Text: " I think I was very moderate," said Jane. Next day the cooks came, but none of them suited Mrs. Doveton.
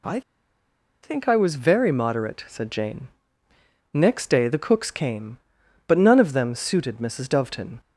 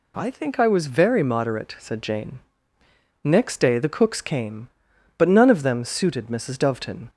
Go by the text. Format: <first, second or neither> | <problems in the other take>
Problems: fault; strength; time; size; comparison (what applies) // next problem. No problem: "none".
second | pauses between "I" and "think"; noticeable; at 0.2 s; 0.82 s long